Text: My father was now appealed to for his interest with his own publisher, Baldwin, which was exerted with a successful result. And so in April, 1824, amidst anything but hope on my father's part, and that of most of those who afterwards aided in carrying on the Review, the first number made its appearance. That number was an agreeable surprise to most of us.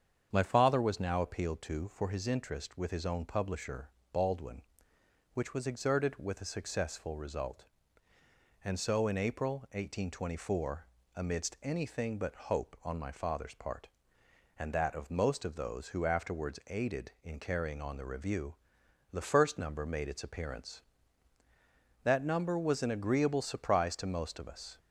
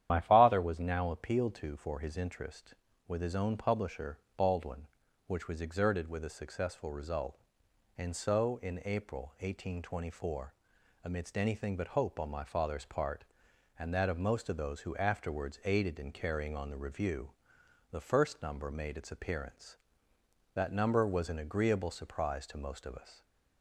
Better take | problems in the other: first | loses the start of "My"; at 0.0 s; 50 ms // starts louder than the rest; strong; until 1.1 s; 10.5 dB; strong in the first

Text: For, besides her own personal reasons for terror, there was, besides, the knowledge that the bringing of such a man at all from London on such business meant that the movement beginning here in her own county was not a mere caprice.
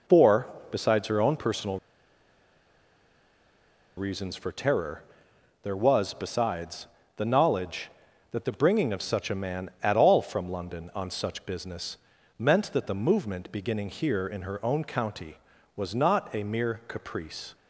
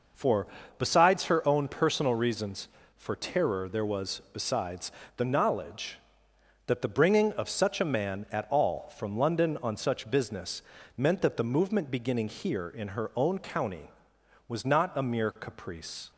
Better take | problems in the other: second | pauses between "personal" and "reasons"; strong; at 1.7 s; 2.1 s long // pauses between "business" and "meant"; at 11.9 s; 0.42 s long; slight in the second

